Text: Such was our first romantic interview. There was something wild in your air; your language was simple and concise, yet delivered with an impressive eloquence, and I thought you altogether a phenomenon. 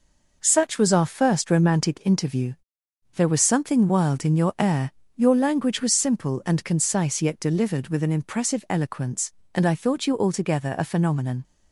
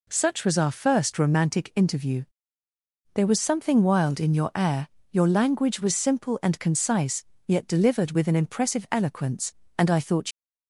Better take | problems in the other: first | stops before "you altogether a phenomenon"; at 10.3 s

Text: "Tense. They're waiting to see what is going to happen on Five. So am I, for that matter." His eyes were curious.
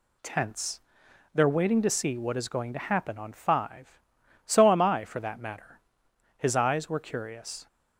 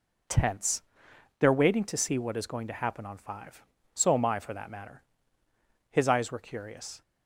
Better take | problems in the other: neither | none

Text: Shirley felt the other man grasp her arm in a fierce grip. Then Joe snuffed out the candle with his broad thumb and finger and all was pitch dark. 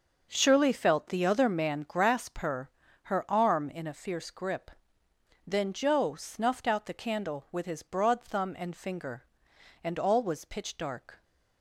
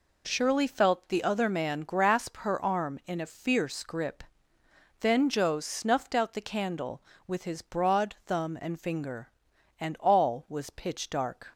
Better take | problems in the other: second | says "her" twice; at 3.0 s

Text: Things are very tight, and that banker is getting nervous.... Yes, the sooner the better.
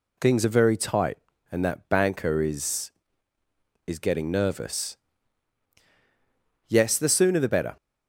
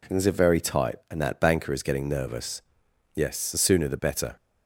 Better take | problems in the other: second | says "is" twice; at 3.8 s

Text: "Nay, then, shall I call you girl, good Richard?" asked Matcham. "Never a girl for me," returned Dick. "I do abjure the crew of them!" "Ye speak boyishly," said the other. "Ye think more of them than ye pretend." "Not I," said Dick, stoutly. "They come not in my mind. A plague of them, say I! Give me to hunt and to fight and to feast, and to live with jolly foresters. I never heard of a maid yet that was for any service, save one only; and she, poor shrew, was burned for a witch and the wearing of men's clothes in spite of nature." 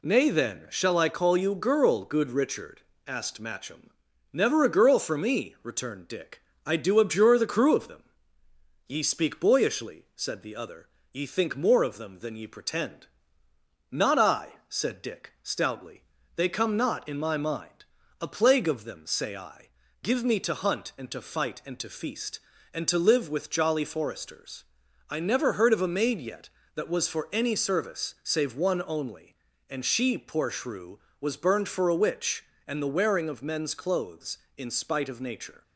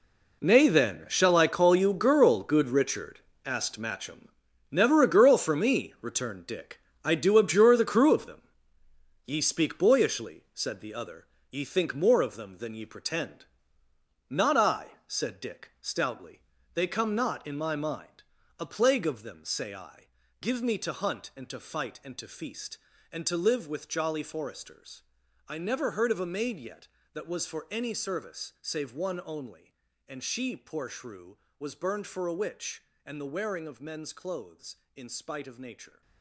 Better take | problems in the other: first | gets quieter; strong; throughout; 12.5 dB

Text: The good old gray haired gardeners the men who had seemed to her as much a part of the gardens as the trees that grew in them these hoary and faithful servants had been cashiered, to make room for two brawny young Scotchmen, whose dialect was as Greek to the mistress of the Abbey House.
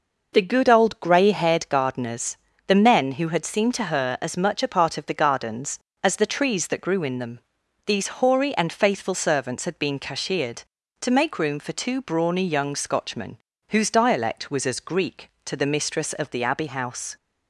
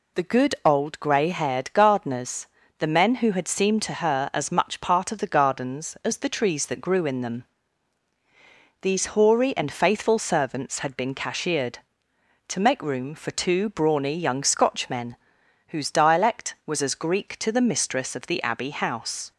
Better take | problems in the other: first | pauses between "gardeners" and "the"; slight; at 2.4 s; 0.32 s long; slight in the first // skips "a"; at 4.7 s // pauses between "them" and "these"; strong; at 7.4 s; 1.3 s long; noticeable in the first

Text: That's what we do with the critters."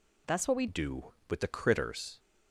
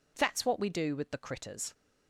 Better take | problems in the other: second | changes voice at "do"; from 0.6 s on; 1.5 s long

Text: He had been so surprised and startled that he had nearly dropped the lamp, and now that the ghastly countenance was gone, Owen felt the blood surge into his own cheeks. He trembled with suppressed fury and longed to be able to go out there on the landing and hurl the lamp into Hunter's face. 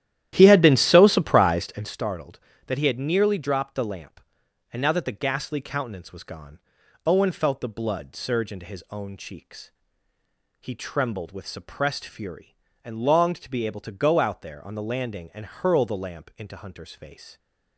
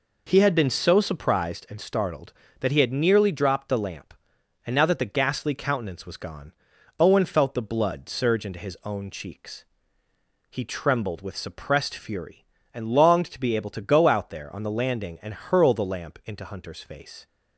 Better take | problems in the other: second | starts louder than the rest; strong; until 2.1 s; 12 dB

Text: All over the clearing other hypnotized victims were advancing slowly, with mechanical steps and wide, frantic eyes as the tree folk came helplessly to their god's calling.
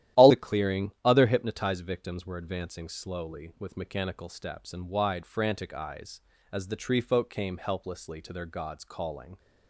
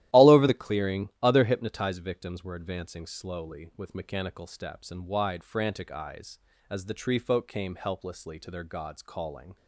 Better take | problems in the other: second | starts louder than the rest; strong; until 1.2 s; 12.5 dB; strong in the second // skips "over"; at 0.3 s

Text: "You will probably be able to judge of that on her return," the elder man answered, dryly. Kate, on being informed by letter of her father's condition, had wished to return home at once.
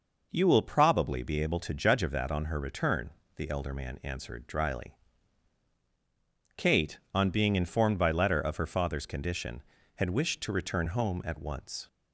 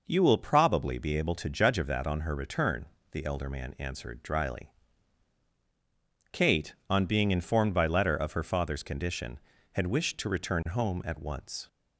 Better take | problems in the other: neither | none

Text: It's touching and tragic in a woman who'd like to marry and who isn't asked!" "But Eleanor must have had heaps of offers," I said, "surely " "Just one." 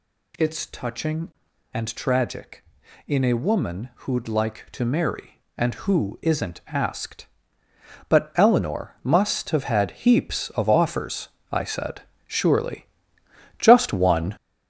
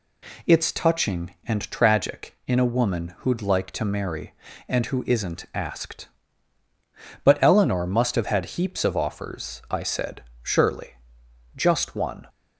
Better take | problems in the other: second | gets louder; slight; throughout; 3 dB

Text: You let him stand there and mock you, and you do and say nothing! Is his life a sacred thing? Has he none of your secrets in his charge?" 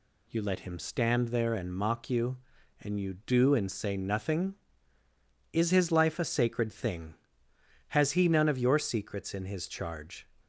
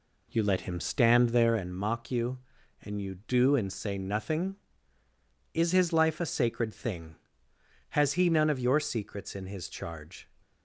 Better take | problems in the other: first | starts louder than the rest; slight; until 1.7 s; 2.5 dB

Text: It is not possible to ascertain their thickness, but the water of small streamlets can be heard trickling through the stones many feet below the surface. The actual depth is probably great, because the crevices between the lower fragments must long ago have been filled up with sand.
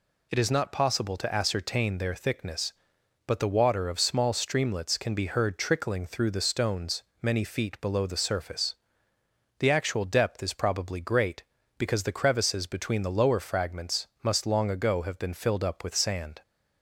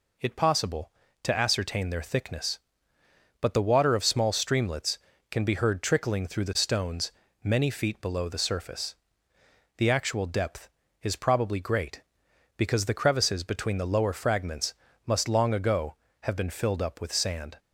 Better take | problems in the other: first | skips "is not"; at 0.3 s // pauses between "stones" and "many"; slight; at 7.1 s; 0.30 s long; slight in the first // pauses between "fragments" and "must"; slight; at 14.7 s; 0.34 s long

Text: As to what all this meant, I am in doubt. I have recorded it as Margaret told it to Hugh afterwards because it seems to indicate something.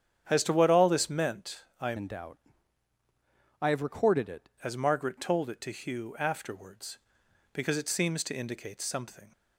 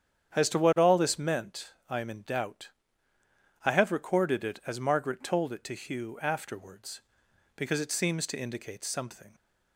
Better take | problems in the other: second | starts louder than the rest; strong; until 1.3 s; 8.5 dB; strong in the second // changes voice from "in" to "it"; from 1.9 to 4.4 s; 2.5 s long

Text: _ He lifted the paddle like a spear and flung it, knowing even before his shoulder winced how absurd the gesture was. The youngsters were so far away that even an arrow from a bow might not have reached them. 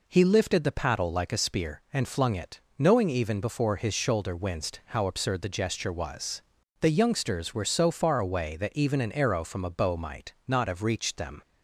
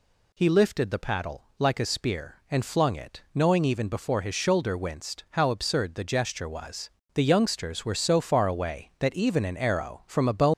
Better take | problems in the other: first | stops before "might not have reached them"; at 10.5 s

